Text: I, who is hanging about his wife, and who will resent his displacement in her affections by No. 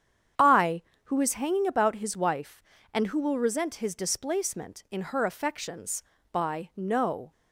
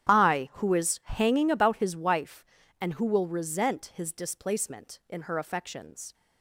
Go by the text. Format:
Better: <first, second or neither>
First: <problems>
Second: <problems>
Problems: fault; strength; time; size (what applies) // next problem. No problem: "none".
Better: first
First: starts louder than the rest; strong; until 1.6 s; 8.5 dB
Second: starts louder than the rest; strong; until 1.1 s; 10.5 dB // stops before "by No"; at 6.1 s